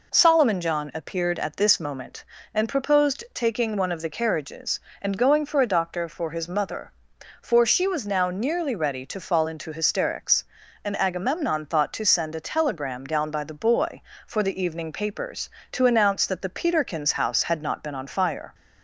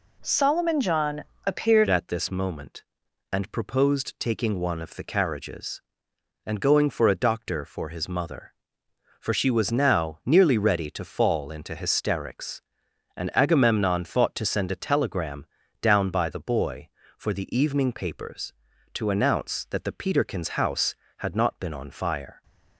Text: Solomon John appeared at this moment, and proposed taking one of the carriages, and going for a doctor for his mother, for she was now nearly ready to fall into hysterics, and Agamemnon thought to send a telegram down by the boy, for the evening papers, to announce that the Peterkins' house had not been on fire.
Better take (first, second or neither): first